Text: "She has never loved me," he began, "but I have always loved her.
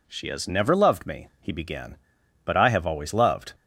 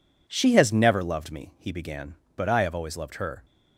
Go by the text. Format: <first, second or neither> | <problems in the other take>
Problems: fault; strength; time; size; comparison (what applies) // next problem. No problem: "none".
second | stops before "her"; at 3.5 s